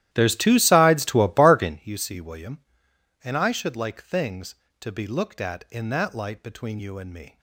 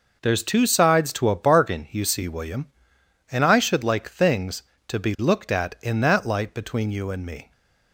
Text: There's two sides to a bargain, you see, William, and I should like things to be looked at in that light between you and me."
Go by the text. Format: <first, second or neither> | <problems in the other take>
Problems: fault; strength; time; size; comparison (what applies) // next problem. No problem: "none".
second | starts louder than the rest; strong; until 1.8 s; 13 dB